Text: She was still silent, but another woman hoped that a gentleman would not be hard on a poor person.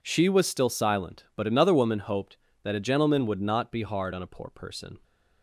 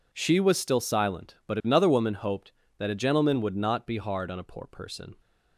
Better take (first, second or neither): neither